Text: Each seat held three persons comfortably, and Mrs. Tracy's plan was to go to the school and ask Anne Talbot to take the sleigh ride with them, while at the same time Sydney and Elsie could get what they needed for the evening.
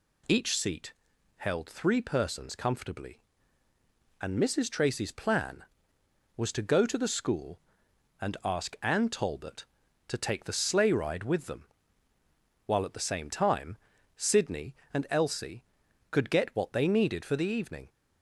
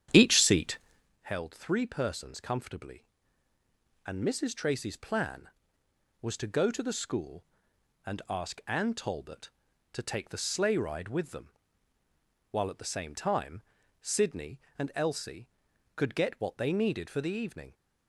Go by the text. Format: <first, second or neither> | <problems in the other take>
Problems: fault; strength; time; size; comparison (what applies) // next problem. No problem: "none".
first | starts louder than the rest; strong; until 1.1 s; 9.5 dB // pauses between "seat" and "held"; at 0.7 s; 0.44 s long; also in the first // pauses between "time" and "Sydney"; at 13.6 s; 0.40 s long; also in the first